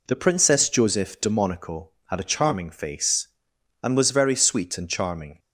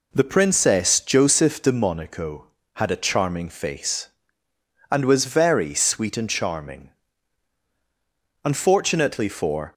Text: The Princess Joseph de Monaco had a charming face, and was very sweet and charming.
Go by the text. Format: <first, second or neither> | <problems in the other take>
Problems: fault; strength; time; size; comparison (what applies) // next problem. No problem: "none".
first | goes on to say "Unfortunately for"; noticeable; from 8.4 s on; 1.3 s long